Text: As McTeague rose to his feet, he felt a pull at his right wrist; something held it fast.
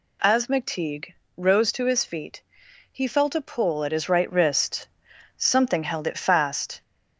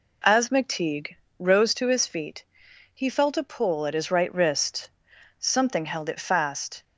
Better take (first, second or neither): second